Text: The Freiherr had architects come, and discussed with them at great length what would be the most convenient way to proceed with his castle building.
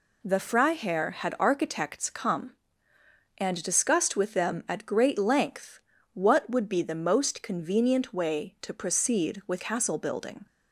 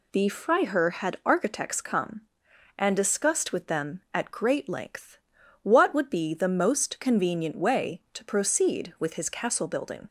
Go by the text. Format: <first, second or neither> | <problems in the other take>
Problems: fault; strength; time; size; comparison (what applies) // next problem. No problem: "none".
second | pauses between "length" and "what"; slight; at 5.7 s; 0.34 s long; also in the second // skips "his"; at 9.5 s